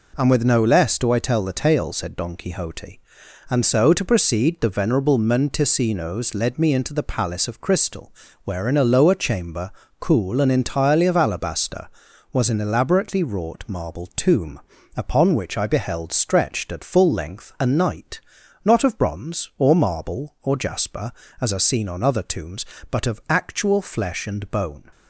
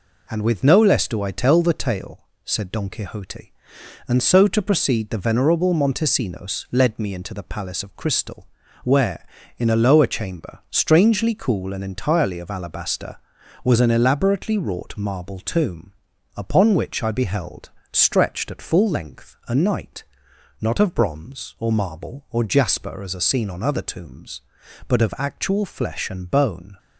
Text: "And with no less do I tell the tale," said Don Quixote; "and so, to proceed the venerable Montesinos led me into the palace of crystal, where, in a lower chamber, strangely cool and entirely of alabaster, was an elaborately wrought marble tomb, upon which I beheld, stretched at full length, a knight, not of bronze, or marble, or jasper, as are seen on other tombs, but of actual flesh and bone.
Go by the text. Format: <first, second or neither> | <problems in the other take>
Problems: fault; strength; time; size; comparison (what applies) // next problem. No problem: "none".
second | skips "strangely"; at 9.8 s